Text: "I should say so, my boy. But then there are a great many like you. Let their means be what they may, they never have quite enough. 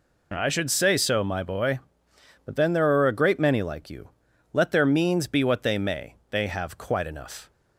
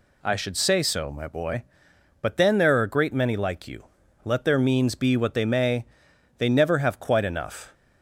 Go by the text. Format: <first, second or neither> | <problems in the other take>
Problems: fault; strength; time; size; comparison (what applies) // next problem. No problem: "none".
second | skips "never"; at 6.4 s